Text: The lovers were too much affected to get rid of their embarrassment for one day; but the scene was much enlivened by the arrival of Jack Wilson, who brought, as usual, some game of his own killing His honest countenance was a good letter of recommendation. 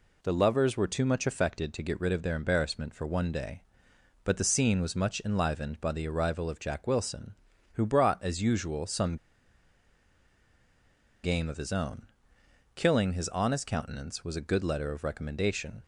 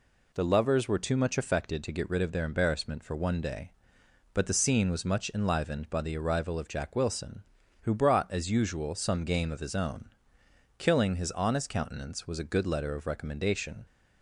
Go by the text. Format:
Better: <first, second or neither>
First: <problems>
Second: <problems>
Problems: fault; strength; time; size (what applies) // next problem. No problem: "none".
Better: second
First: pauses between "some" and "game"; strong; at 9.1 s; 2.0 s long // pauses between "own" and "killing"; noticeable; at 12.0 s; 0.66 s long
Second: pauses between "own" and "killing"; noticeable; at 10.1 s; 0.66 s long